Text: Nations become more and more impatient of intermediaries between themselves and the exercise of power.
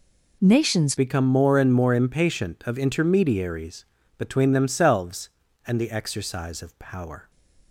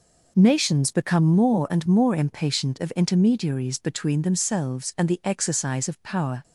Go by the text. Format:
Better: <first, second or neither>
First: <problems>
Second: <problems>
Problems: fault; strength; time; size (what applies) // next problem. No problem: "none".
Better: second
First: changes voice at "become"; from 0.9 s on; 6.4 s long // pauses between "intermediaries" and "between"; slight; at 3.8 s; 0.32 s long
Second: none